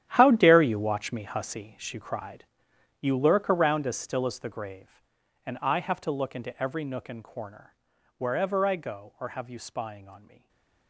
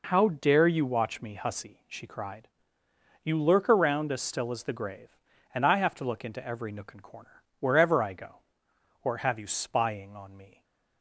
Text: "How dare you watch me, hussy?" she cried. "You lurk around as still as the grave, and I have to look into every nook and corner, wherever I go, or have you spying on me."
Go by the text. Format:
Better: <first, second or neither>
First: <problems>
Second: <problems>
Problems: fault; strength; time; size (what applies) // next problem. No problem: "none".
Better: second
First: gets quieter; strong; throughout; 15 dB // stays silent after the last word; slight; from 10.2 s on; 0.6 s long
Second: none